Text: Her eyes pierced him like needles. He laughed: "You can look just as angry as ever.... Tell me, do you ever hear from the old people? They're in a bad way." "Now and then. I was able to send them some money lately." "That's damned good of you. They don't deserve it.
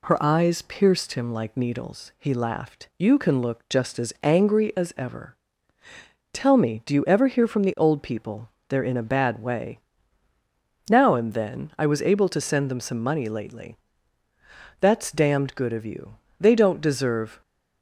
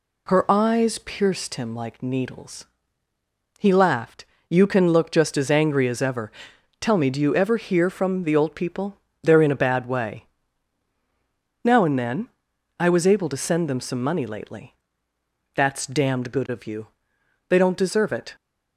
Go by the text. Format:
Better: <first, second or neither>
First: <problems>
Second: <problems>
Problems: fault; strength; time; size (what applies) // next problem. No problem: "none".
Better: second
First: stops before "it"; at 17.4 s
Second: none